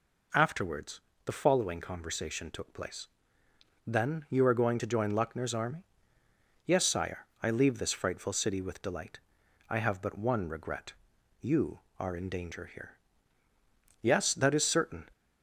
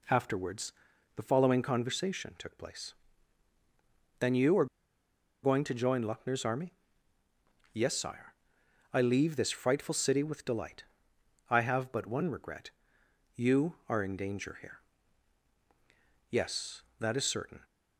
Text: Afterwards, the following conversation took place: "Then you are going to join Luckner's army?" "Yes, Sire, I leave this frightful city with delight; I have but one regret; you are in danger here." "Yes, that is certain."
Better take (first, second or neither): first